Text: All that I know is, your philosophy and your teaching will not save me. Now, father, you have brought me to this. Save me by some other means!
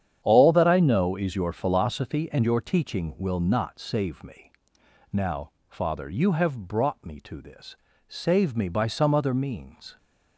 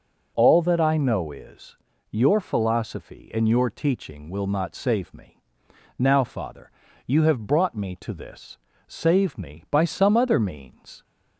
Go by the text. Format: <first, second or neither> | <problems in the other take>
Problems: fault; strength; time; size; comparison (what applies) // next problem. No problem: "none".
second | gets quieter; strong; throughout; 11 dB